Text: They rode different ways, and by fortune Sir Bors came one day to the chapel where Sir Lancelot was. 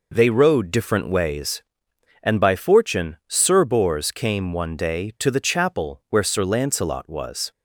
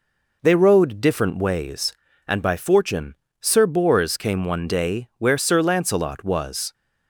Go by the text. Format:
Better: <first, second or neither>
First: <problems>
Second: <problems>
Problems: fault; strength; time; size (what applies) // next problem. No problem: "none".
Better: first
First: none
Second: pauses between "fortune" and "Sir"; slight; at 3.1 s; 0.26 s long // skips "to the chapel"; at 5.1 s